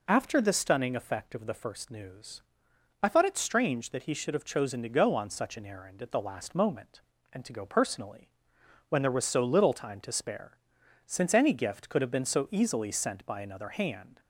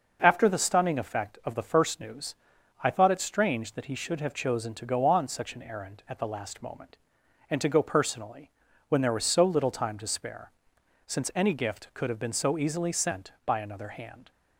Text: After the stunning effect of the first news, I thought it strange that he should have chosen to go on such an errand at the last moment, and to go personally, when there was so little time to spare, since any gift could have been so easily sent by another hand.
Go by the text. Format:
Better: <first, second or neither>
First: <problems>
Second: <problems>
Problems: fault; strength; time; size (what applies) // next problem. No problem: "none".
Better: neither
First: none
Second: none